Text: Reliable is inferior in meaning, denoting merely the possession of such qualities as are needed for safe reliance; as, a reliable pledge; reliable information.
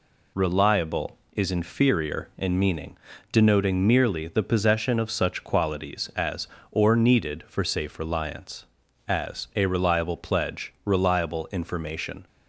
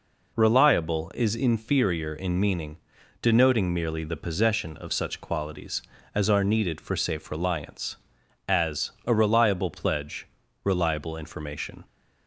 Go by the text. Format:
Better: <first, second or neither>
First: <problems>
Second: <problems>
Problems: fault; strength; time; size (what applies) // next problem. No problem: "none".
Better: second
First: says "or" for "are"; at 6.6 s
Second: none